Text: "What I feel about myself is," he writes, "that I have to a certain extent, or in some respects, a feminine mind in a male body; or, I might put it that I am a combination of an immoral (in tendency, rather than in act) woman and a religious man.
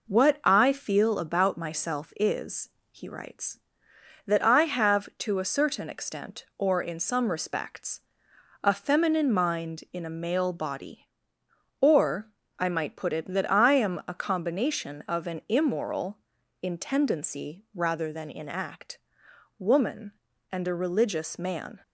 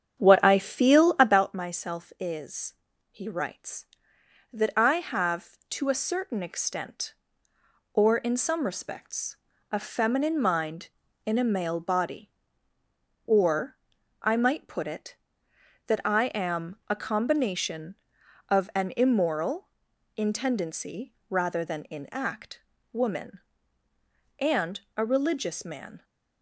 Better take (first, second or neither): first